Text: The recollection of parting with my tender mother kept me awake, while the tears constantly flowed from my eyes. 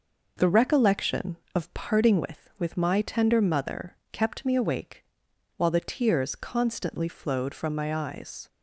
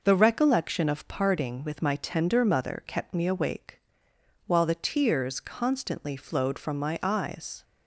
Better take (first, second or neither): second